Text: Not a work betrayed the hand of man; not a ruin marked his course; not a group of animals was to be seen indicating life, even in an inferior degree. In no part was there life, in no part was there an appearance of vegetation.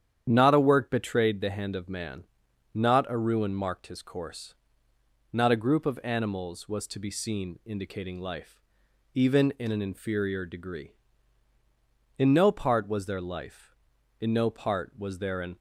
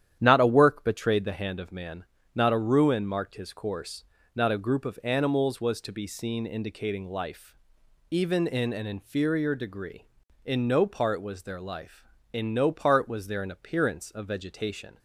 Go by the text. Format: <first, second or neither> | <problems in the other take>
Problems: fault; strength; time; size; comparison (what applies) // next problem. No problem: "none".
second | starts louder than the rest; strong; until 1.3 s; 9 dB; strong in the second // stops before "appearance of vegetation"; at 15.5 s